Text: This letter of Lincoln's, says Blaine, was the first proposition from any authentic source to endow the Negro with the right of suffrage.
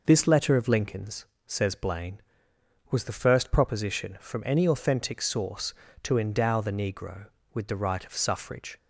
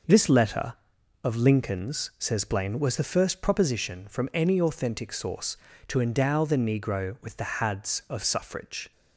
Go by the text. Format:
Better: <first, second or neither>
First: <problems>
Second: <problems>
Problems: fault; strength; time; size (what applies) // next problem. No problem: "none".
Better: first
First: none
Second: says "hads" for "right"; at 7.5 s